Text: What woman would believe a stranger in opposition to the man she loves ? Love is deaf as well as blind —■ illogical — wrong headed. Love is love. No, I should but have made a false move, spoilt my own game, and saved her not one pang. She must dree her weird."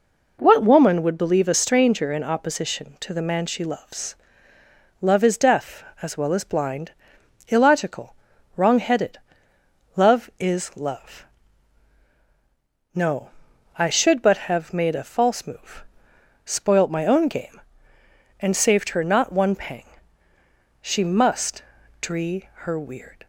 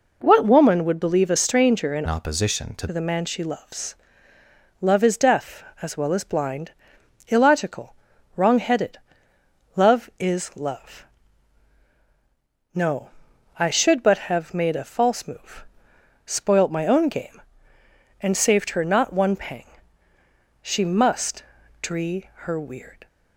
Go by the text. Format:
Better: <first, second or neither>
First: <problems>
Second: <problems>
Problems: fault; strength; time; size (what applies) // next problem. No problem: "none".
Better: first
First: pauses between "must" and "dree"; slight; at 21.6 s; 0.36 s long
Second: changes voice from "opposition" to "to"; from 2.0 to 2.8 s; 0.8 s long // pauses between "must" and "dree"; slight; at 21.4 s; 0.36 s long